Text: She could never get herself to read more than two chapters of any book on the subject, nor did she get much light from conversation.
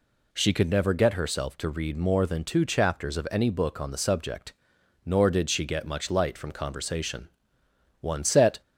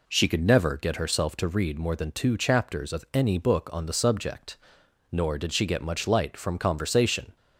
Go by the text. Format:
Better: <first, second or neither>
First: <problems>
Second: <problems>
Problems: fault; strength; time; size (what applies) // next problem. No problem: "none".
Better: second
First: goes on to say "One set"; from 8.0 s on; 0.60 s long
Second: none